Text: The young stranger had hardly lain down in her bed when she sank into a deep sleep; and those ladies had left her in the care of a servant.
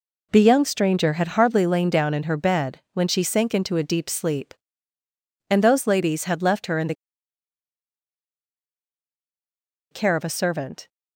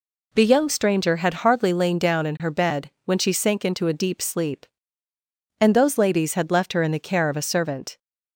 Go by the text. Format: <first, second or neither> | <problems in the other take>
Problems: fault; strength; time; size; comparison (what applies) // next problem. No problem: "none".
second | pauses between "the" and "care"; strong; at 6.9 s; 2.9 s long